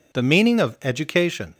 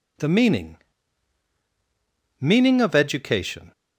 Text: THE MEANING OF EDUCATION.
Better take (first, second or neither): first